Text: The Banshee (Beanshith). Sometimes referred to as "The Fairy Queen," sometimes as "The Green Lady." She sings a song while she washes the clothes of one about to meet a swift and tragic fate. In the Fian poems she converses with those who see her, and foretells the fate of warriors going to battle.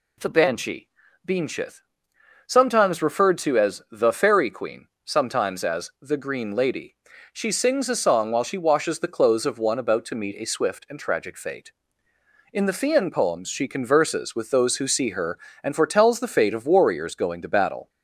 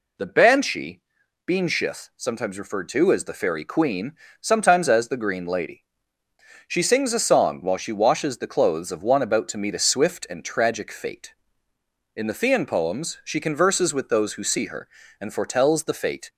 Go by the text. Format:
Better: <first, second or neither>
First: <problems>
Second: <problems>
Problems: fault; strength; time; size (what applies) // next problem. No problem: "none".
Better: first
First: none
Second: stops before "of warriors going to battle"; at 16.2 s